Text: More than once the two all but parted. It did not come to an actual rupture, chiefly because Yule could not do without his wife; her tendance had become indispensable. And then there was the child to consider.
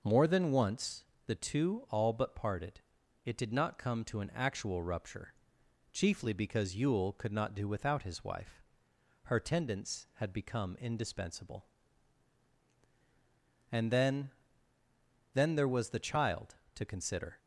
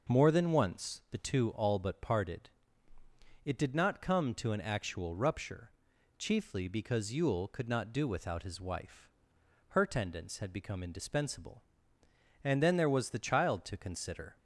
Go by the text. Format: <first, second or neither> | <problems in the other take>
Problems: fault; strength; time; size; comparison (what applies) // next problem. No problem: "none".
second | pauses between "once" and "the"; slight; at 1.0 s; 0.22 s long // says "then" twice; at 15.3 s